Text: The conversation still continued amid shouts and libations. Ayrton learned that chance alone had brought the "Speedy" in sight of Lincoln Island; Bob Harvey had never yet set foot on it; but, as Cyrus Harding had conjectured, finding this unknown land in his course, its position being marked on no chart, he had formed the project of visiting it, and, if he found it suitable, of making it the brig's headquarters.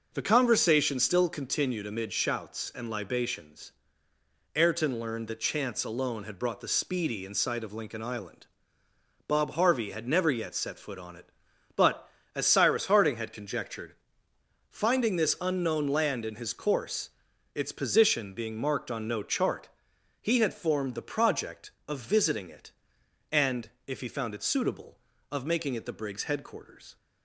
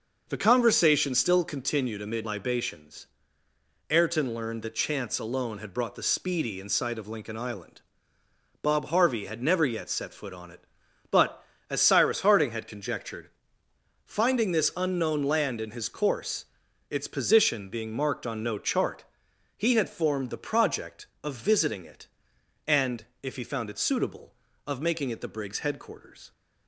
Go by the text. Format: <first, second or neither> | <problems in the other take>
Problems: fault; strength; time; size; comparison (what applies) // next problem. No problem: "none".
first | skips "shouts and"; at 2.2 s